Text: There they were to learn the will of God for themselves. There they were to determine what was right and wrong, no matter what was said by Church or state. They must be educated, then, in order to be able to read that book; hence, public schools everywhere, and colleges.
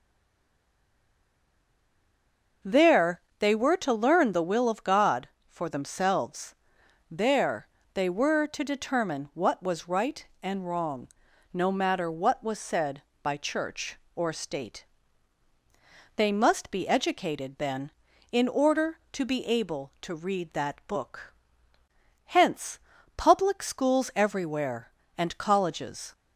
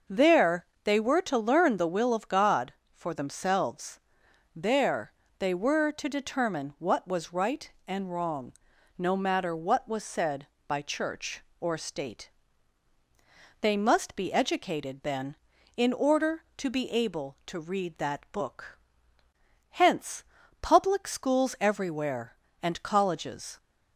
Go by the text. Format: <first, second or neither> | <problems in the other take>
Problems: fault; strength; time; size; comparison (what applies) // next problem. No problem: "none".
second | stays silent before the first word; strong; until 2.6 s; 2.6 s long // pauses between "There" and "they"; slight; at 3.2 s; 0.16 s long; slight in the second // pauses between "There" and "they"; slight; at 7.6 s; 0.26 s long; slight in the second